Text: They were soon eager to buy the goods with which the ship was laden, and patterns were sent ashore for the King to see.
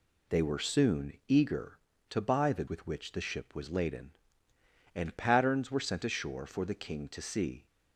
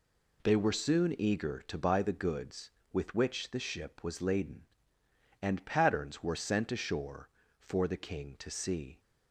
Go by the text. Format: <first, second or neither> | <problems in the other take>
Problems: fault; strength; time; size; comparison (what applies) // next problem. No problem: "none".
second | skips "goods"; at 2.6 s